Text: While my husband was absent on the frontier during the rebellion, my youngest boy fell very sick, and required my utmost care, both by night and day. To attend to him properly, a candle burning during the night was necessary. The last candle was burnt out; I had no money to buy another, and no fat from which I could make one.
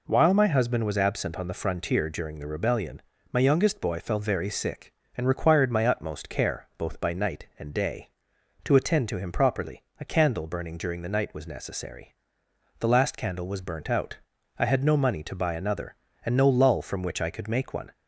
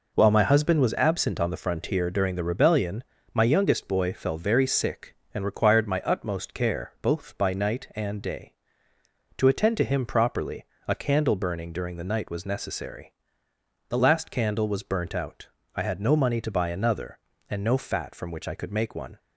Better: second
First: says "lull" for "fat"; at 16.4 s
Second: none

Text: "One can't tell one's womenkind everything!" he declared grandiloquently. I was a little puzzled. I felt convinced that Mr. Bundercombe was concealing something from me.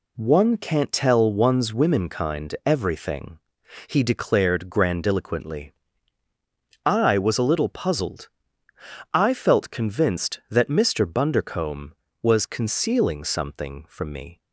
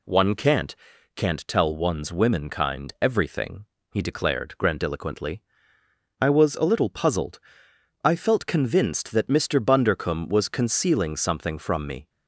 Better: first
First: none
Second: says "can't" twice; at 1.1 s

